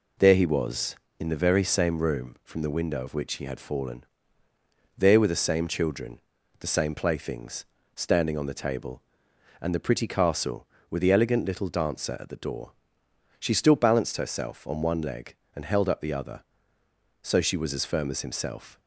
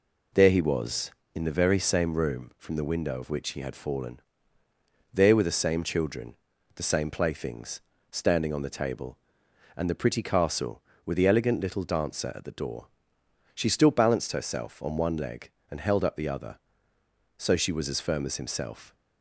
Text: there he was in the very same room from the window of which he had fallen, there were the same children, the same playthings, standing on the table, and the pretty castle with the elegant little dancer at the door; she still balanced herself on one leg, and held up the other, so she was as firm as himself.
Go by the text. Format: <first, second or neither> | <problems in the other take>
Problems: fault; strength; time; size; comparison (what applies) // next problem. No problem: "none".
neither | none